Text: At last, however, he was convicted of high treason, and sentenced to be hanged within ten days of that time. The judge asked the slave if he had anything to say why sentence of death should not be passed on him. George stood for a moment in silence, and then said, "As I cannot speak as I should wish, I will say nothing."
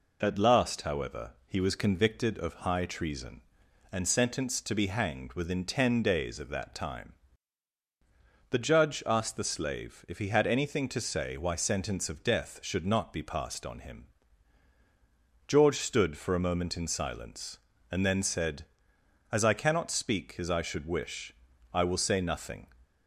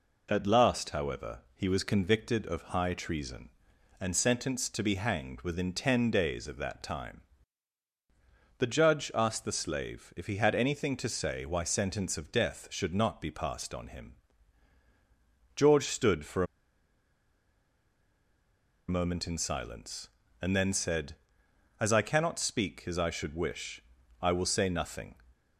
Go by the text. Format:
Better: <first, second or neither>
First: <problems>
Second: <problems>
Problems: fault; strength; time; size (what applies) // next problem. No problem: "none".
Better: first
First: none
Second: pauses between "for" and "a"; strong; at 16.4 s; 2.4 s long